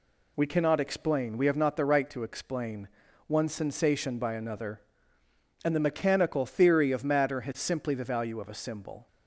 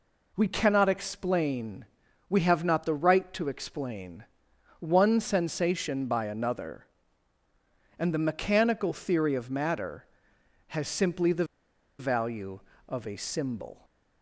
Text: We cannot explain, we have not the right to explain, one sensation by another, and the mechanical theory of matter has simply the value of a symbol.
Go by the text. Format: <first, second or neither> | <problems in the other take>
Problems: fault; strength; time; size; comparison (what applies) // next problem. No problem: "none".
first | pauses between "the" and "value"; noticeable; at 11.4 s; 0.55 s long